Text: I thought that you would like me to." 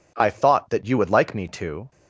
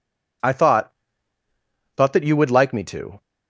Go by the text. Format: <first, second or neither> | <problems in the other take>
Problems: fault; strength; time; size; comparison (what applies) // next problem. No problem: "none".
first | says "thought" twice; at 1.9 s